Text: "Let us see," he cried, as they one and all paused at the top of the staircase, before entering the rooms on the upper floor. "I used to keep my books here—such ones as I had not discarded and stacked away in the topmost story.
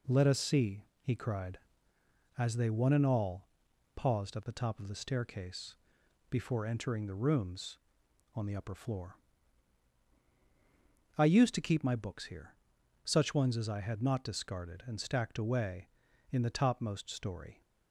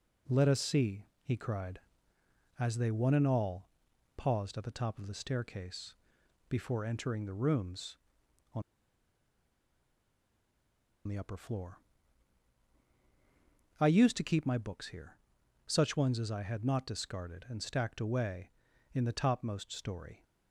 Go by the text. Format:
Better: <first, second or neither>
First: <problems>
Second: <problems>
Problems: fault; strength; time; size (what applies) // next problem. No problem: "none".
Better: first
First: pauses between "all" and "paused"; noticeable; at 3.4 s; 0.48 s long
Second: pauses between "all" and "paused"; noticeable; at 3.6 s; 0.48 s long // pauses between "on" and "the"; strong; at 8.6 s; 2.4 s long